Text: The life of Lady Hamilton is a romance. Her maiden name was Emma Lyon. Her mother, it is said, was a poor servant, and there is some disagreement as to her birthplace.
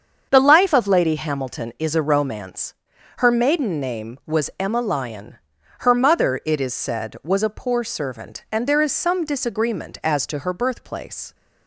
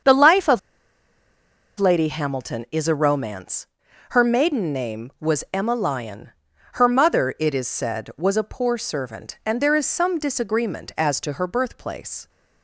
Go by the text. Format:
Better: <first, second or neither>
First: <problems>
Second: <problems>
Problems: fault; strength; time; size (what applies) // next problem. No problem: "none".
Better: first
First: starts louder than the rest; until 1.3 s; 7 dB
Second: starts louder than the rest; until 2.2 s; 7 dB // pauses between "of" and "Lady"; at 0.5 s; 1.2 s long